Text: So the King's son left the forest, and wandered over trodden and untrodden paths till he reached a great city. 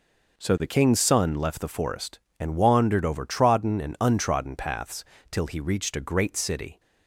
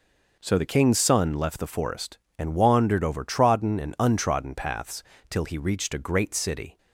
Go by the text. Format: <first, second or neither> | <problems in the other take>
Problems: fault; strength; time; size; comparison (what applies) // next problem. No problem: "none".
neither | pauses between "paths" and "till"; slight; the same in both